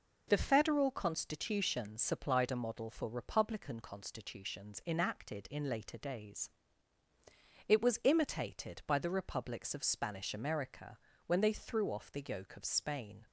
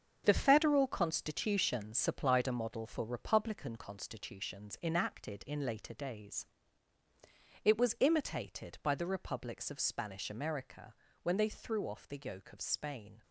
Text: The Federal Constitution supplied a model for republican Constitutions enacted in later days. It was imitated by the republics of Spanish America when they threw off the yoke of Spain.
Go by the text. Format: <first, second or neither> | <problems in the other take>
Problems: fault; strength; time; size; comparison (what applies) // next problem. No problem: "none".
first | gets quieter; strong; throughout; 9 dB // pauses between "America" and "when"; slight; at 10.9 s; 0.26 s long; slight in the first